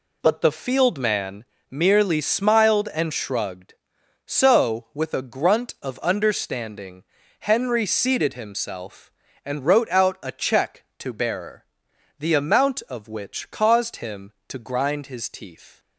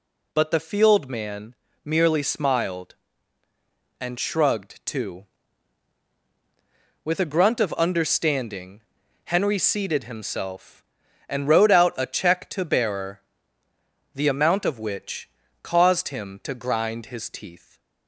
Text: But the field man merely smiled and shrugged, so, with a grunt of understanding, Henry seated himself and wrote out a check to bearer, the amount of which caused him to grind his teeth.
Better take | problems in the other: first | pauses between "man" and "merely"; slight; at 1.5 s; 0.30 s long; slight in the first // says "too" for "so"; at 4.8 s // pauses between "which" and "caused"; slight; at 15.2 s; 0.34 s long

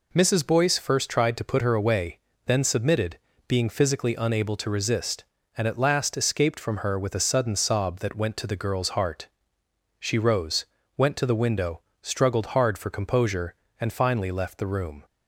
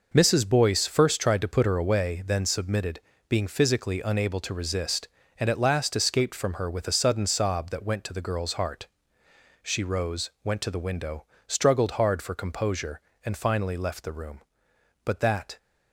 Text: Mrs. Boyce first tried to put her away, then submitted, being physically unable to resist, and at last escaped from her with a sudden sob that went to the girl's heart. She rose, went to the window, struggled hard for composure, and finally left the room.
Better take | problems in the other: first | goes on to say "But that"; from 15.0 s on; 0.52 s long

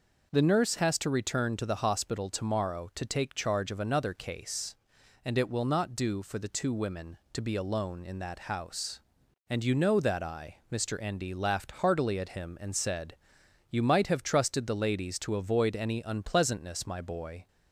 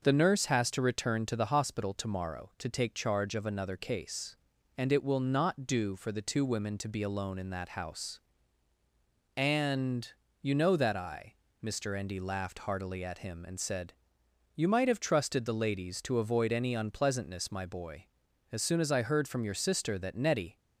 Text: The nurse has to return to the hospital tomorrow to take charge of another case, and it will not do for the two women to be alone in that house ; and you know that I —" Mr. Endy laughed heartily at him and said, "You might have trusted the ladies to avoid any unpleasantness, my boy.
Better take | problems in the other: first | pauses between "and" and "you"; slight; at 10.0 s; 0.32 s long // goes on to say "As soon as I heard from your sister that Nettie"; strong; from 18.5 s on; 2.0 s long

